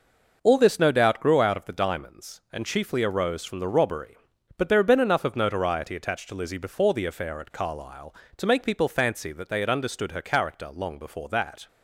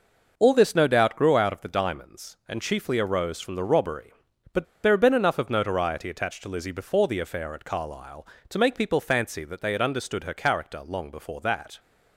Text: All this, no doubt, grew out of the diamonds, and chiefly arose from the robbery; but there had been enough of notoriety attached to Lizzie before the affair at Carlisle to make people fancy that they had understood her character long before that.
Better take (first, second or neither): first